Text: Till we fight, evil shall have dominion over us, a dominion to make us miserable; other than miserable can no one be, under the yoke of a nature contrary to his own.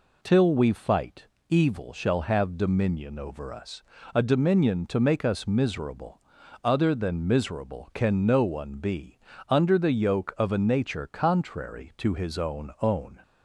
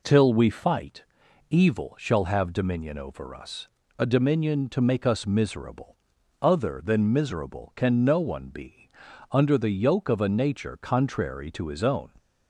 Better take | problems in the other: second | says "own" twice; at 12.8 s

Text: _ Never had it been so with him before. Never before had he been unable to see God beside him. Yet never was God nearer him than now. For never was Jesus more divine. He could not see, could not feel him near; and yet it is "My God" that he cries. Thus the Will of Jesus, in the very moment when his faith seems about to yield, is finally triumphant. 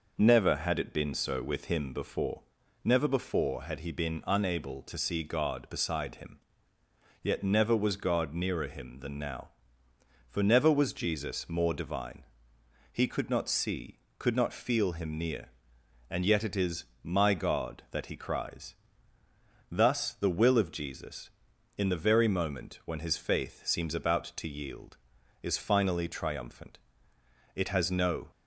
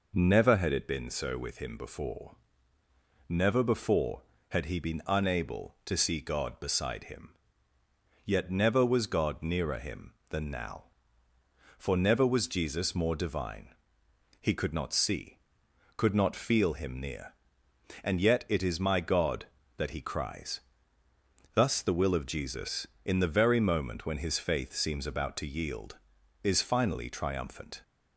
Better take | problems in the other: second | pauses between "is" and "My"; slight; at 16.8 s; 0.18 s long // goes on to say "It has no"; noticeable; from 27.5 s on; 0.76 s long

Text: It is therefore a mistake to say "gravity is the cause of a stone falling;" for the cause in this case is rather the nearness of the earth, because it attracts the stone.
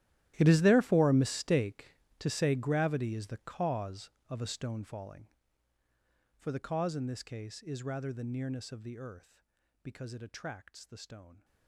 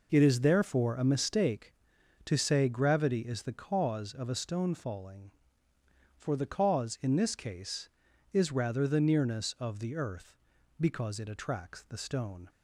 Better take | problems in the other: second | gets quieter; strong; throughout; 19.5 dB

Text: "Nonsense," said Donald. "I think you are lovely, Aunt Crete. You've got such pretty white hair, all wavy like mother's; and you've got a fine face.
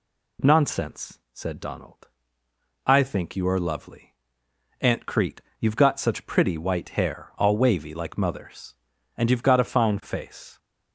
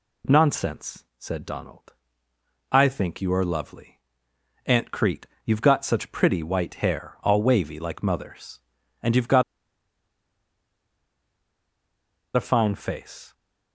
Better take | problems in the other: first | pauses between "got" and "a"; strong; at 9.4 s; 2.9 s long

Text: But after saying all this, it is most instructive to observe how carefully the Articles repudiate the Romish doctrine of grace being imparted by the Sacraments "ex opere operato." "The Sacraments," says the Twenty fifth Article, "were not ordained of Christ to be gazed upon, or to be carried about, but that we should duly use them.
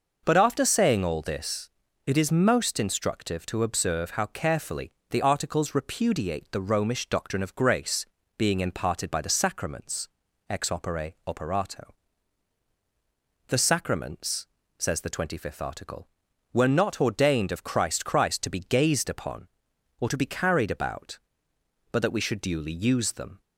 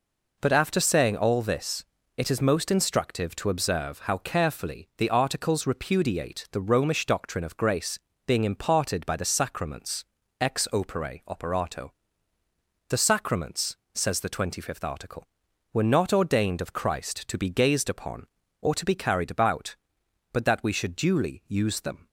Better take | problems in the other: second | pauses between "carefully" and "the"; slight; at 4.9 s; 0.18 s long // pauses between "grace" and "being"; slight; at 8.0 s; 0.32 s long; slight in the second // pauses between "Sacraments" and "ex"; at 10.0 s; 0.40 s long; slight in the second // says "Christ" twice; at 18.0 s

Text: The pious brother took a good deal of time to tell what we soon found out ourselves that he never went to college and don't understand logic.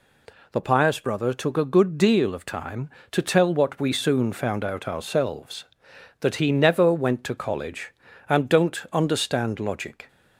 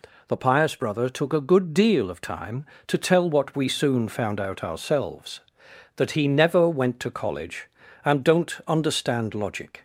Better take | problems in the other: neither | none

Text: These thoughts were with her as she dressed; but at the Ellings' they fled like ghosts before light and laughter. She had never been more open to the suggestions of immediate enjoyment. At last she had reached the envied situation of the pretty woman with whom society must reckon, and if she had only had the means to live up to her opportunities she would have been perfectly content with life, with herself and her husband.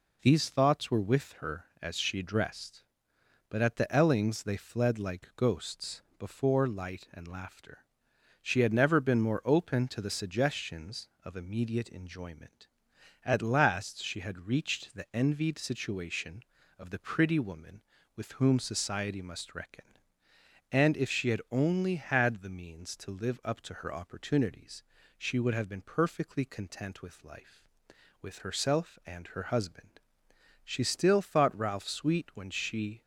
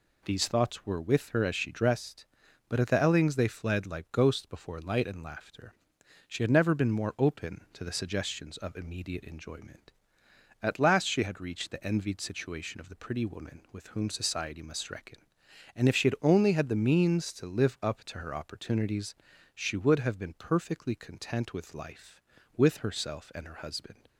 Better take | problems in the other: second | pauses between "ghosts" and "before"; slight; at 6.0 s; 0.16 s long // pauses between "opportunities" and "she"; slight; at 24.8 s; 0.34 s long; also in the second // goes on to say "She still thought Ralph sweet when she"; strong; from 30.6 s on; 2.3 s long

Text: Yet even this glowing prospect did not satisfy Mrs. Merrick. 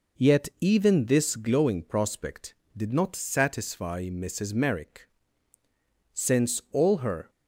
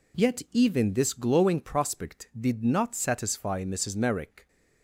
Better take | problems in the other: second | goes on to say "Since all her"; noticeable; from 6.1 s on; 1.1 s long

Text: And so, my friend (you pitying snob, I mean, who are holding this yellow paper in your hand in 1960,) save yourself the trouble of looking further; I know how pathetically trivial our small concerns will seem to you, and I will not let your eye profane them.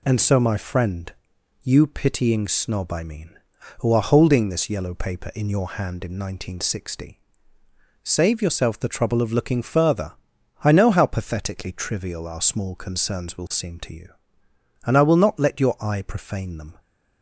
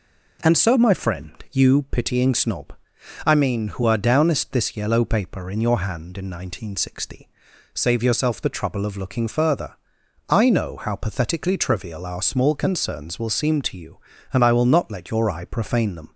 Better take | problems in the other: first | says "downest" for "holding"; at 3.9 s

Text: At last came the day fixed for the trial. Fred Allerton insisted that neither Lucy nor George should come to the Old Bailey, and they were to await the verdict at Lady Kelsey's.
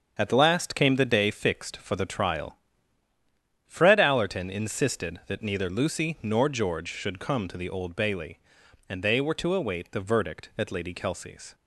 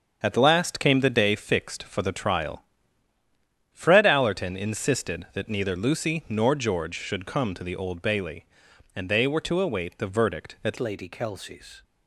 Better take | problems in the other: first | starts louder than the rest; strong; until 1.2 s; 7.5 dB; strong in the first // changes voice at "Lady"; from 10.7 s on; 1.1 s long

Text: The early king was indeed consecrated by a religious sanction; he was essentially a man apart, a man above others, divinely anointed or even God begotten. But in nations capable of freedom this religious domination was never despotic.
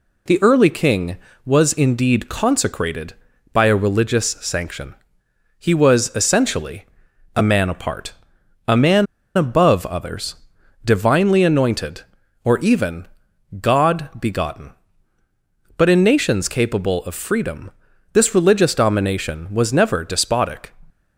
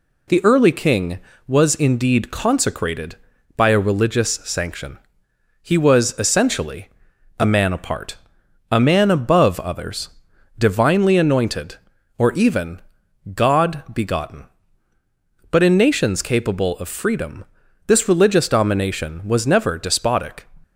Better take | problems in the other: second | pauses between "essentially" and "a"; noticeable; at 6.8 s; 0.52 s long; noticeable in the second // pauses between "man" and "above"; slight; at 9.0 s; 0.30 s long // pauses between "even" and "God"; noticeable; at 13.0 s; 0.54 s long; noticeable in the second // pauses between "freedom" and "this"; at 17.7 s; 0.44 s long; also in the second

